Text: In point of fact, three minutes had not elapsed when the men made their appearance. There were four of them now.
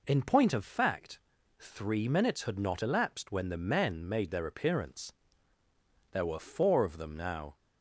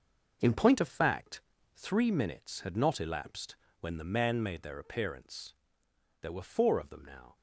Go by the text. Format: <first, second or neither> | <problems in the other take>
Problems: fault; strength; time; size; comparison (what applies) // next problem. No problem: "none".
first | gets quieter; strong; throughout; 8.5 dB // pauses between "elapsed" and "when"; slight; at 3.5 s; 0.26 s long